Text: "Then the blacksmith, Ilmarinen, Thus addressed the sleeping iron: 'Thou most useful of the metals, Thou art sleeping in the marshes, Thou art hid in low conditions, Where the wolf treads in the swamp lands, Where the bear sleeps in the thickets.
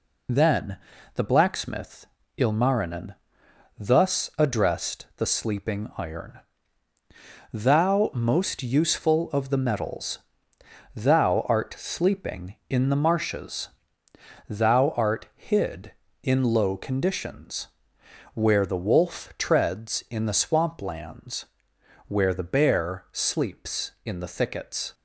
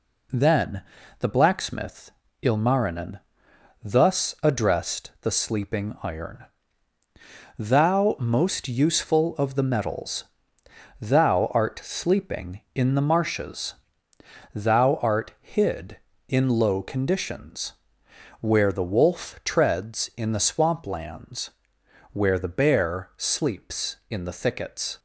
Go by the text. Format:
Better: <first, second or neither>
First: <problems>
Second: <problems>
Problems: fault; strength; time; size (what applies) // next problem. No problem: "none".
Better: second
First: loses the start of "Then"; at 0.2 s; 40 ms // pauses between "Then" and "the"; slight; at 0.7 s; 0.36 s long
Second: pauses between "Then" and "the"; slight; at 0.8 s; 0.36 s long